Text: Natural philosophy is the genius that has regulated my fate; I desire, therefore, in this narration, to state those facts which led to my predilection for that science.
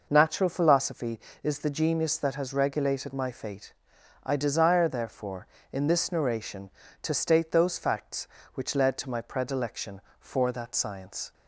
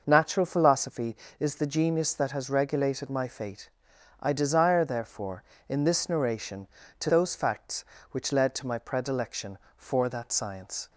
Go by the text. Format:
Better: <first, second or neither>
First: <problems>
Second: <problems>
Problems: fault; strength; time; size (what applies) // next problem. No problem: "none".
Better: first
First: none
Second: skips "state"; at 7.0 s